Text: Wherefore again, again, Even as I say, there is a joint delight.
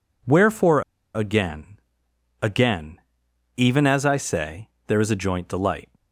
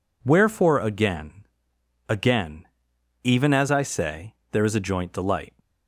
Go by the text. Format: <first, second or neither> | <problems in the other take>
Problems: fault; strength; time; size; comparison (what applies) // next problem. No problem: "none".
second | pauses between "Wherefore" and "again"; slight; at 0.8 s; 0.32 s long